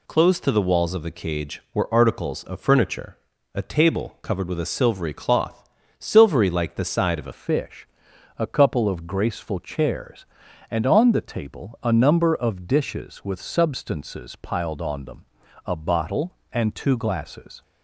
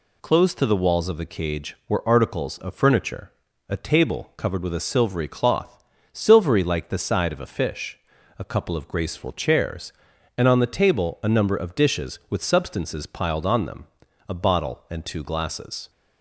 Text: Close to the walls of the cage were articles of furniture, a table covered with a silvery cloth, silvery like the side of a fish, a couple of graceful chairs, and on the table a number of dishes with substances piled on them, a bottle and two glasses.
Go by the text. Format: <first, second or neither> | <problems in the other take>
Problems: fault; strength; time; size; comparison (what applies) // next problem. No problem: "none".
second | changes voice at "fish"; from 7.3 s on; 10.3 s long